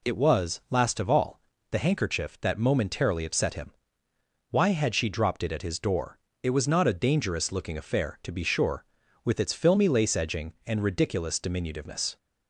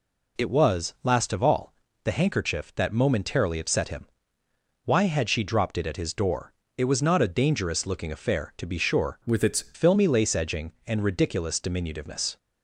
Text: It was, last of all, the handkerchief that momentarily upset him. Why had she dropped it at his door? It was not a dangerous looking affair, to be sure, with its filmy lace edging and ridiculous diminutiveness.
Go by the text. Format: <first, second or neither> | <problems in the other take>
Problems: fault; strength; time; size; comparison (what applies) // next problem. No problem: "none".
first | changes voice from "with" to "its"; from 9.2 to 9.7 s; 0.5 s long